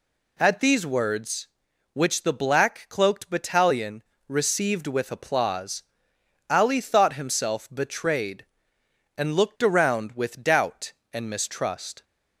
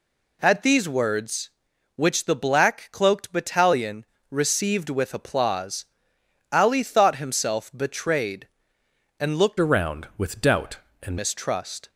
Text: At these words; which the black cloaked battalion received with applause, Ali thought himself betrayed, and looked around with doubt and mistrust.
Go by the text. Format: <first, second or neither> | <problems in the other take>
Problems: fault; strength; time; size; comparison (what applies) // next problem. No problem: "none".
first | pauses between "battalion" and "received"; slight; at 4.0 s; 0.26 s long; slight in the first // changes voice from "around" to "and"; from 9.6 to 11.1 s; 1.5 s long